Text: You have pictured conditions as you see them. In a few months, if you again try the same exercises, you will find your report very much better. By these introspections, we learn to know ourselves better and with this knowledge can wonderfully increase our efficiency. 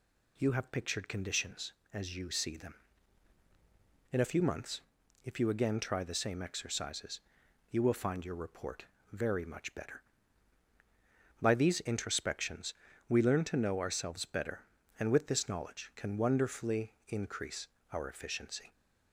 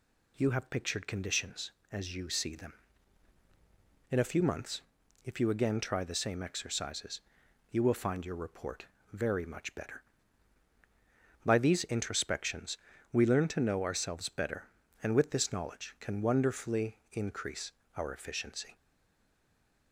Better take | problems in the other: first | pauses between "report" and "very"; slight; at 8.8 s; 0.26 s long; slight in the first // pauses between "wonderfully" and "increase"; slight; at 16.9 s; 0.16 s long; slight in the first // pauses between "increase" and "our"; slight; at 17.7 s; 0.24 s long; slight in the first // stays silent after the last word; from 18.7 s on; 1.2 s long

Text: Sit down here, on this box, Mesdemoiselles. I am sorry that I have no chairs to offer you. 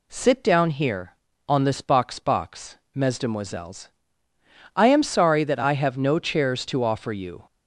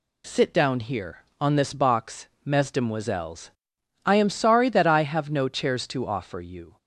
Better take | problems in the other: second | says "box" twice; at 2.1 s

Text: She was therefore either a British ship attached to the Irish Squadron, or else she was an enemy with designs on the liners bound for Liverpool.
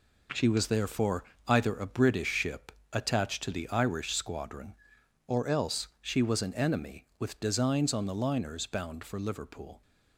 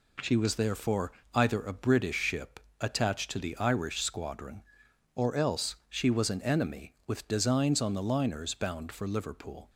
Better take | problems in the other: second | gets quieter; strong; throughout; 8.5 dB // pauses between "therefore" and "either"; slight; at 1.2 s; 0.24 s long; slight in the second // pauses between "ship" and "attached"; slight; at 2.7 s; 0.20 s long; slight in the second

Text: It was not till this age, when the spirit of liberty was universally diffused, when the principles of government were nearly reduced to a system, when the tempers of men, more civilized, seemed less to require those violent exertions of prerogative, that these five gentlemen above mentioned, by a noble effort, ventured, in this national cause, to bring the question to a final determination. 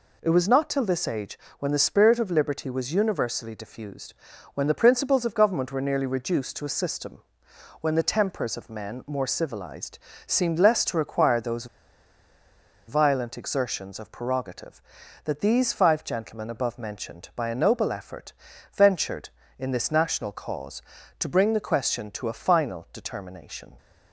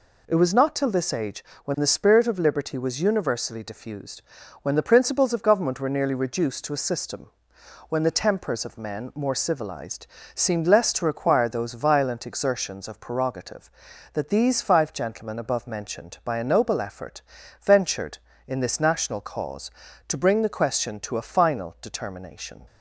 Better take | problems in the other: second | pauses between "those" and "violent"; at 11.6 s; 1.2 s long

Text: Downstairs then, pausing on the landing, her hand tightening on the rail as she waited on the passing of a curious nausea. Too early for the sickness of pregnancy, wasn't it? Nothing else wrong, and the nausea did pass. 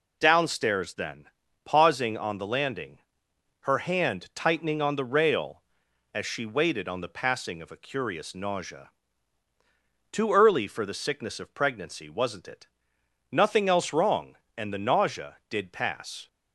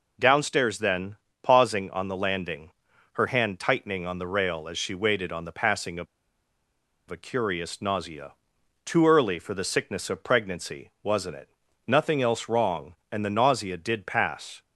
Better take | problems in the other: first | pauses between "of" and "a"; at 6.0 s; 1.0 s long

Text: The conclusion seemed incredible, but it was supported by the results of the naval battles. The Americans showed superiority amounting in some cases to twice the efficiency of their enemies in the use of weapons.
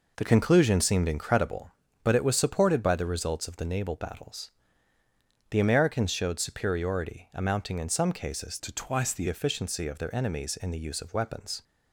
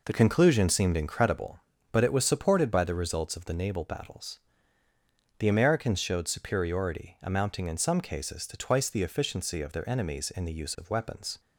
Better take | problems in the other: second | changes voice from "to" to "the"; from 8.5 to 9.2 s; 0.7 s long

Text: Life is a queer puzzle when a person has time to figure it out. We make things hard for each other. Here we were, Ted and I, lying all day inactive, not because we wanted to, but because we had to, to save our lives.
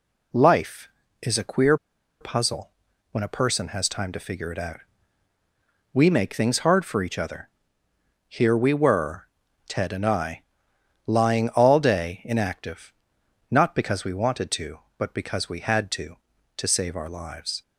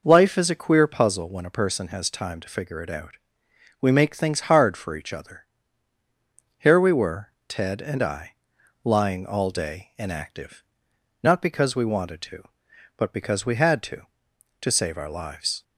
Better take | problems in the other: second | pauses between "queer" and "puzzle"; at 1.7 s; 0.45 s long // pauses between "puzzle" and "when"; at 2.7 s; 0.40 s long

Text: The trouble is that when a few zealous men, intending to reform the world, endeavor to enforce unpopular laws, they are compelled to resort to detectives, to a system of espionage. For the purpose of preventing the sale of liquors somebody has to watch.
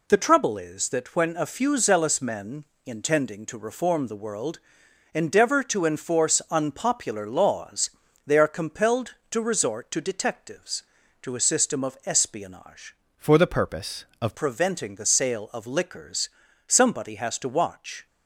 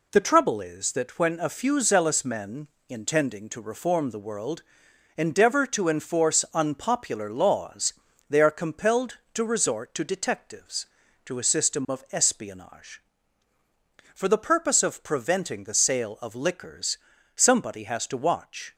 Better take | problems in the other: second | changes voice from "For" to "of"; from 13.1 to 14.3 s; 1.2 s long // pauses between "liquors" and "somebody"; at 16.2 s; 0.38 s long; also in the second

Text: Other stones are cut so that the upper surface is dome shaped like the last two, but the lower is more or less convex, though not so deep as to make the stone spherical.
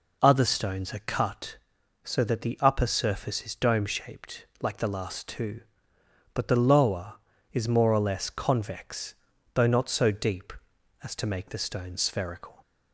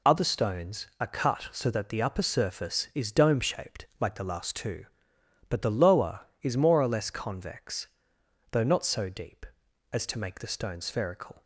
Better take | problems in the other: neither | pauses between "shaped" and "like"; slight; the same in both

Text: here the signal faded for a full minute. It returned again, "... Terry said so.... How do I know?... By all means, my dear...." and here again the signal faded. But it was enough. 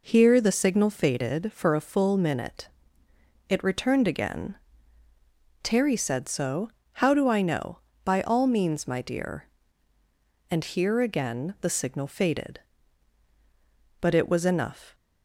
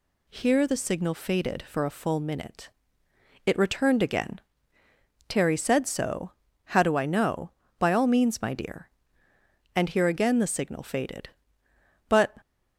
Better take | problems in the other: first | stops before "it was enough"; at 12.4 s

